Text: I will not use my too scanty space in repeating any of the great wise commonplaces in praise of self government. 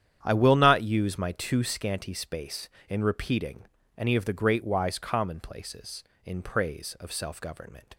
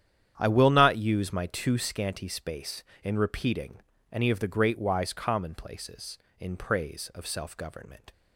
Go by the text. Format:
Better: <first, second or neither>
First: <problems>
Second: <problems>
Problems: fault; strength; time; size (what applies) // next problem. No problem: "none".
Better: neither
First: starts louder than the rest; strong; until 1.2 s; 9.5 dB // pauses between "repeating" and "any"; slight; at 3.6 s; 0.32 s long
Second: starts louder than the rest; strong; until 1.3 s; 9.5 dB // pauses between "repeating" and "any"; slight; at 3.8 s; 0.32 s long